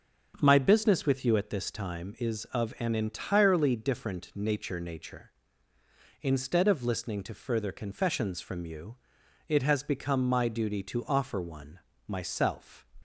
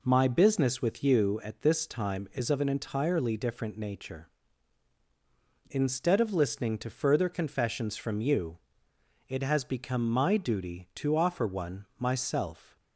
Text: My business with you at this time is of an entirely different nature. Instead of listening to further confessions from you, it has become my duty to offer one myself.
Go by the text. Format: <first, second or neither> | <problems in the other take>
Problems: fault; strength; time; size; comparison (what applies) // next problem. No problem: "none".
second | starts louder than the rest; until 1.4 s; 7 dB // says "nature" twice; at 4.7 s // pauses between "one" and "myself"; slight; at 11.7 s; 0.28 s long